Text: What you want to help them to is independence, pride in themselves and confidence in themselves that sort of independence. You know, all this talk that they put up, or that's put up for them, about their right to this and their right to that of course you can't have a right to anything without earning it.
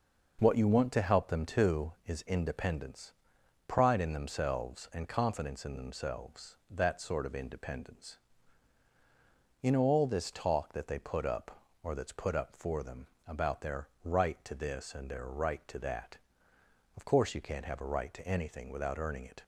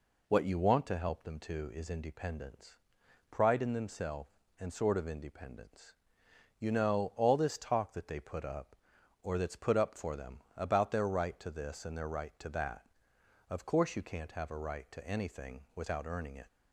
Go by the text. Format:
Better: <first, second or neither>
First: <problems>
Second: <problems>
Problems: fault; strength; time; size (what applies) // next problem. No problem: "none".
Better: first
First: none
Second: skips "confidence in themselves that"; at 4.7 s // pauses between "anything" and "without"; slight; at 15.5 s; 0.16 s long